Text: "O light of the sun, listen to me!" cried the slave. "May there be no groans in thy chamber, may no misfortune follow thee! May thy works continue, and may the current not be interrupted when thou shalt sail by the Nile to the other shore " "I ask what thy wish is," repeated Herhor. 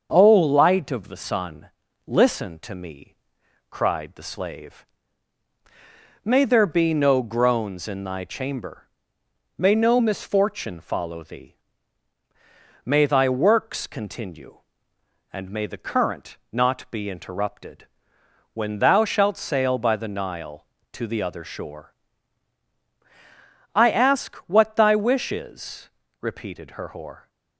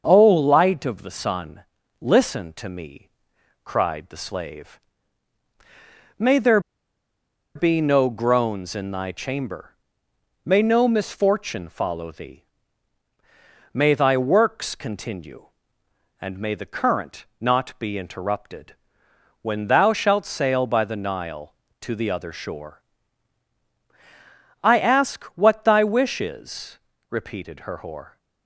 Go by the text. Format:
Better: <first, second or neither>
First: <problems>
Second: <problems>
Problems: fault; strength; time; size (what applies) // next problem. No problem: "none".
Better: first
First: starts louder than the rest; until 1.1 s; 6.5 dB // pauses between "interrupted" and "when"; noticeable; at 17.8 s; 0.66 s long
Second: starts louder than the rest; until 1.0 s; 6.5 dB // pauses between "there" and "be"; noticeable; at 6.5 s; 0.96 s long // pauses between "interrupted" and "when"; noticeable; at 18.7 s; 0.66 s long